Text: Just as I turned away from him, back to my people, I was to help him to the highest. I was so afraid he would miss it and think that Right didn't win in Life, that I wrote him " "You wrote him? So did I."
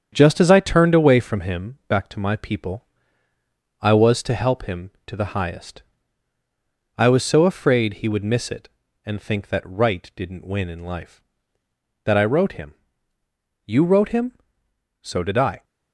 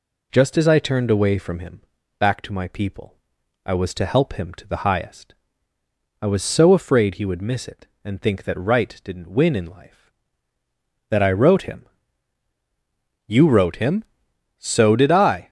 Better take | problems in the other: second | gets quieter; strong; throughout; 14 dB

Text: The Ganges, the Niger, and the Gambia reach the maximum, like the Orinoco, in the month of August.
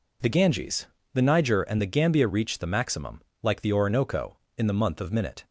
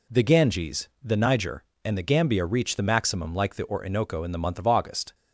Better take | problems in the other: second | says "Minute" for "August"; at 5.1 s

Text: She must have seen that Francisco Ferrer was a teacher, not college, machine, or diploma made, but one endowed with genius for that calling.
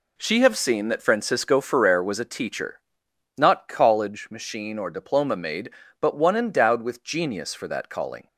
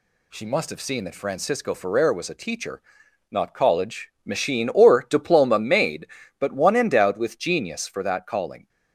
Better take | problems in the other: second | skips "must"; at 0.4 s

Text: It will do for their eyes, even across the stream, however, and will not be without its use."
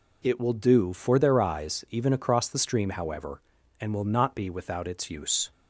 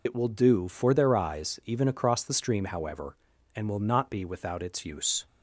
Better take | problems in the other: first | loses the start of "It"; at 0.0 s; 70 ms

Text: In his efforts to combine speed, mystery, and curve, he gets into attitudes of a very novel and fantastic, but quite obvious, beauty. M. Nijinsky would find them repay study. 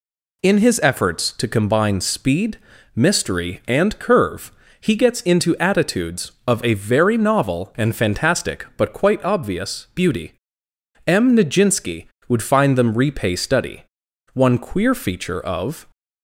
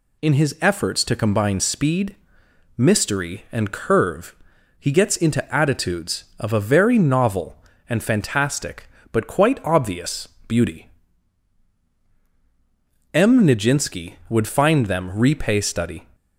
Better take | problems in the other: second | goes on to say "One queer feature of"; from 14.3 s on; 1.5 s long

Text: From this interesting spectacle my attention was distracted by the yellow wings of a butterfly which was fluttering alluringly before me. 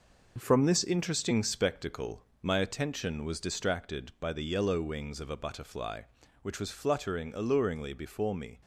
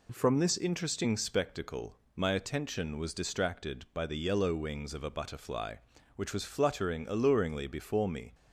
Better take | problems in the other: second | gets quieter; throughout; 6.5 dB // pauses between "spectacle" and "my"; slight; at 2.2 s; 0.22 s long; slight in the second

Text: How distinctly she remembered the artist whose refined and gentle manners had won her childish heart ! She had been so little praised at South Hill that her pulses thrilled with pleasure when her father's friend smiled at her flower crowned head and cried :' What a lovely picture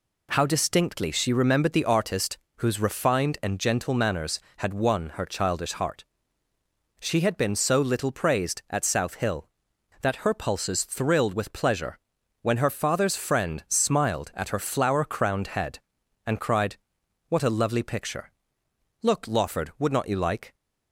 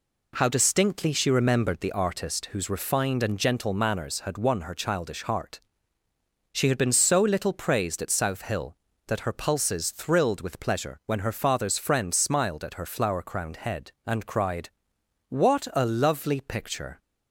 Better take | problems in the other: second | pauses between "artist" and "whose"; slight; at 2.3 s; 0.20 s long // pauses between "pleasure" and "when"; at 11.9 s; 0.44 s long // goes on to say "Look Lawford would not you like"; from 19.0 s on; 1.5 s long

